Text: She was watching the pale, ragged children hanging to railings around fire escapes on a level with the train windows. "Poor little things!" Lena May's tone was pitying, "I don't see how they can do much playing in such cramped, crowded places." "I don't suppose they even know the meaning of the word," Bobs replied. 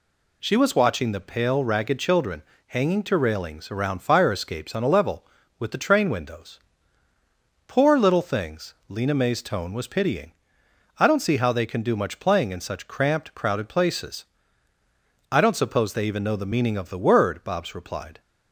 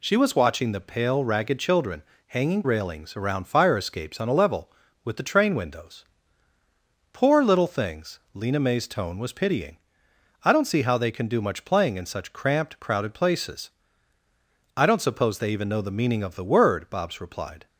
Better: first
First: pauses between "children" and "hanging"; slight; at 2.4 s; 0.28 s long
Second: pauses between "children" and "hanging"; slight; at 2.0 s; 0.28 s long // skips "to"; at 2.6 s

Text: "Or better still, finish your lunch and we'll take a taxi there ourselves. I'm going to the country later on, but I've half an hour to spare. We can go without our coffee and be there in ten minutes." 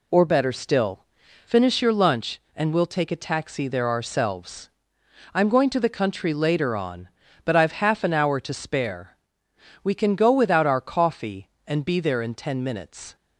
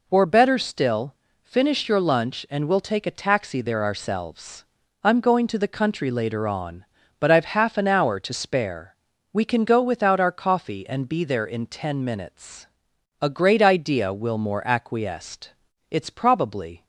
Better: first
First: none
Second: goes on to say "A great idea Wilmore acquiesced It's probably"; strong; from 13.2 s on; 3.6 s long

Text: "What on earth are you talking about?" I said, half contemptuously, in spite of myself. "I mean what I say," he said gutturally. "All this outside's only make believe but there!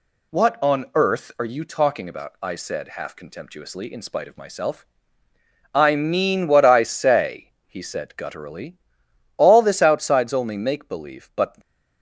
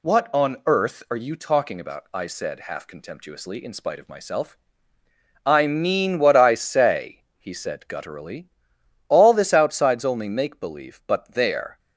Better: second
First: stops before "there"; at 11.6 s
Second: none

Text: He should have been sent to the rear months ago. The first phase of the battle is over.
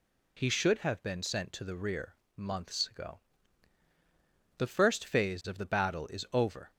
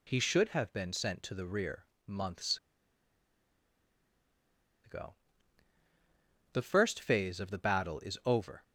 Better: first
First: pauses between "rear" and "months"; slight; at 2.1 s; 0.22 s long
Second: pauses between "rear" and "months"; slight; at 1.8 s; 0.22 s long // pauses between "months" and "ago"; strong; at 2.5 s; 2.2 s long

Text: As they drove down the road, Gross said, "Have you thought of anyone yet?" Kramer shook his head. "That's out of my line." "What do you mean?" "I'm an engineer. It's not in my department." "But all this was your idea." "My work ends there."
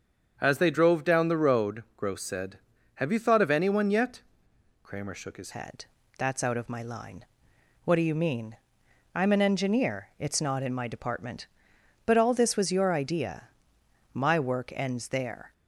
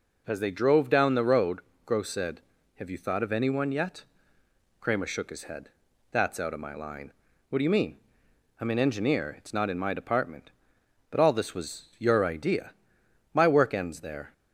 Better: second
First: starts louder than the rest; until 1.3 s; 6.5 dB // changes voice at "head"; from 5.5 s on; 10.0 s long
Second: none

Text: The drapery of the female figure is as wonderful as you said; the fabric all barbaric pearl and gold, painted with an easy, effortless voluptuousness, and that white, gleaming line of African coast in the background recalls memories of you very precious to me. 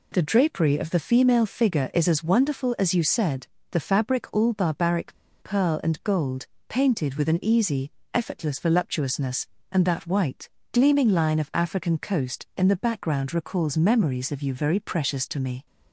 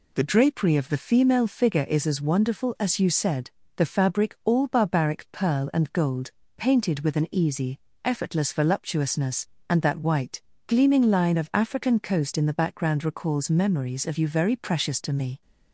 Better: second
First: pauses between "barbaric" and "pearl"; slight; at 5.1 s; 0.28 s long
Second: none

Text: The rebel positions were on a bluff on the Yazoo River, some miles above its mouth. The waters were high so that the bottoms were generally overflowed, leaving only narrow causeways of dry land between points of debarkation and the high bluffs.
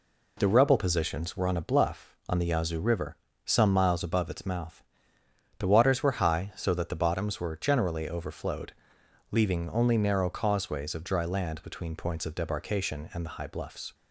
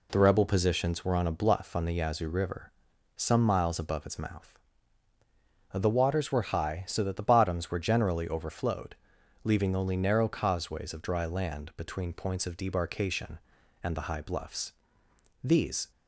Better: first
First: none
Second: goes on to say "These"; slight; from 15.4 s on; 0.48 s long

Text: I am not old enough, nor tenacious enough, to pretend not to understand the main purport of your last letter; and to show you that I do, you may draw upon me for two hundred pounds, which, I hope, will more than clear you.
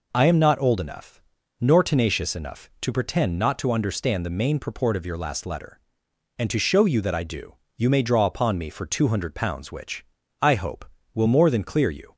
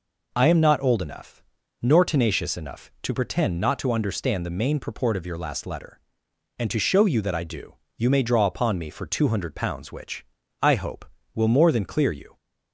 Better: neither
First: none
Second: none

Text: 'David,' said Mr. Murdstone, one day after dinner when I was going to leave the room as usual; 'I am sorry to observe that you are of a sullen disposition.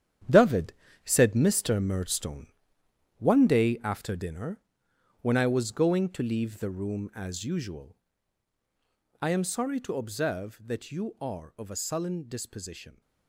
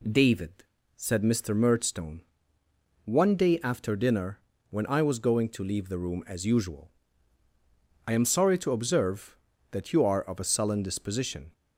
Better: second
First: gets quieter; strong; throughout; 11 dB // pauses between "dinner" and "when"; noticeable; at 4.6 s; 0.60 s long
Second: pauses between "dinner" and "when"; slight; at 4.4 s; 0.30 s long

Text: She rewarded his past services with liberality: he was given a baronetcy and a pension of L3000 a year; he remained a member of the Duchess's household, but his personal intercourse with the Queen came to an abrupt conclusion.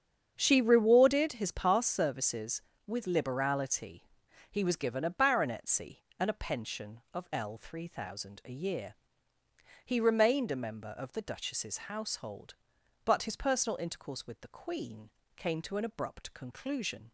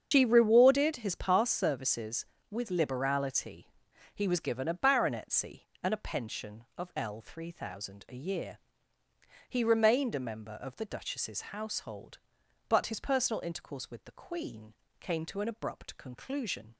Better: first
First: starts louder than the rest; strong; until 1.3 s; 7.5 dB // pauses between "Queen" and "came"; slight; at 15.0 s; 0.28 s long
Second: loses the start of "She"; at 0.1 s; 105 ms // starts louder than the rest; strong; until 1.1 s; 7.5 dB // pauses between "Queen" and "came"; slight; at 14.7 s; 0.28 s long

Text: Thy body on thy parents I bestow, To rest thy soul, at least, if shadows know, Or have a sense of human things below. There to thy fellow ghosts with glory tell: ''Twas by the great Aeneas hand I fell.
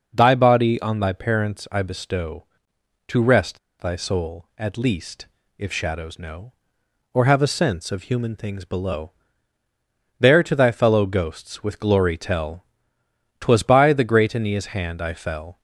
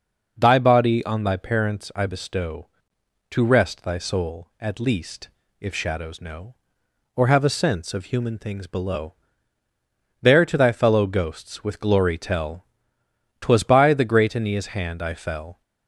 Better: second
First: pauses between "rest" and "thy"; slight; at 3.5 s; 0.23 s long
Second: none

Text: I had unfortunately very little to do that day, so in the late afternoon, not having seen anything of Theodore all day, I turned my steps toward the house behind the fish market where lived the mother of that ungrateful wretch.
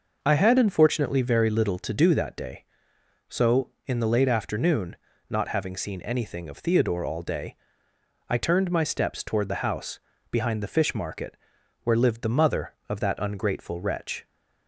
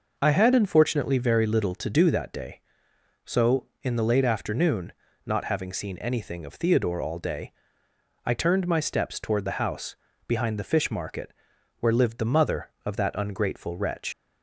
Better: first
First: pauses between "house" and "behind"; slight; at 9.9 s; 0.32 s long // pauses between "market" and "where"; noticeable; at 11.3 s; 0.48 s long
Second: pauses between "house" and "behind"; slight; at 9.9 s; 0.32 s long // pauses between "market" and "where"; noticeable; at 11.3 s; 0.48 s long // leaves "wretch" unfinished; at 14.1 s; 105 ms

